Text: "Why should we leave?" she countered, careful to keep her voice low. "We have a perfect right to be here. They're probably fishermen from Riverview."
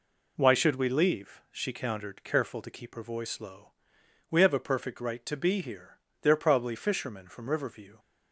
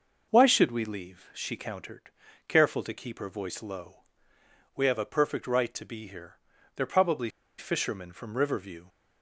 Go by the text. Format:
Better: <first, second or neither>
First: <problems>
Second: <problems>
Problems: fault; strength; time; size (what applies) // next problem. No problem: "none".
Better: first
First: none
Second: pauses between "probably" and "fishermen"; slight; at 7.2 s; 0.28 s long